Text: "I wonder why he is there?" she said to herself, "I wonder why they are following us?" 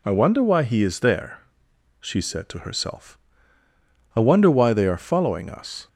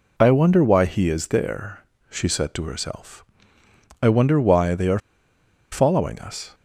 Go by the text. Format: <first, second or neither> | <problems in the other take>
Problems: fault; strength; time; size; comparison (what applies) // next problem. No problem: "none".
first | pauses between "are" and "following"; noticeable; at 4.9 s; 0.73 s long